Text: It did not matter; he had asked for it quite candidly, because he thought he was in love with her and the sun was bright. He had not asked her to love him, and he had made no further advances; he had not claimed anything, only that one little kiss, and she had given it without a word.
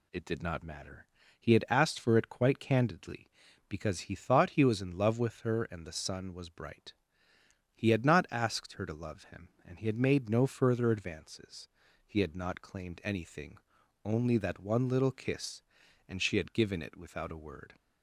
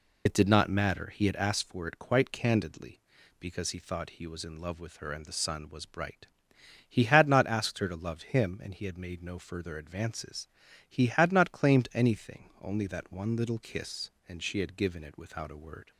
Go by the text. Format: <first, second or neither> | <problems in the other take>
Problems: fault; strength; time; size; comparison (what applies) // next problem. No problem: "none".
first | loses the start of "It"; at 0.2 s; 65 ms